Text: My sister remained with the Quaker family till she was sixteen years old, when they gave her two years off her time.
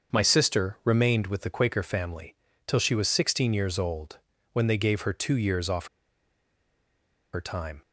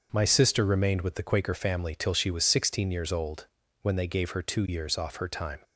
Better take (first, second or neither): second